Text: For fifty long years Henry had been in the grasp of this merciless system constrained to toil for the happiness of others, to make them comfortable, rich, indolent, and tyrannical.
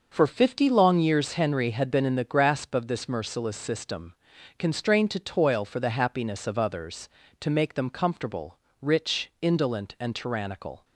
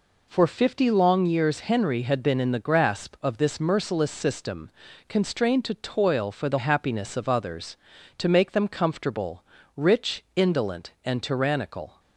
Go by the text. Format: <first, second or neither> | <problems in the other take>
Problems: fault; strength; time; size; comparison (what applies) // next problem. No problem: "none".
neither | pauses between "system" and "constrained"; the same in both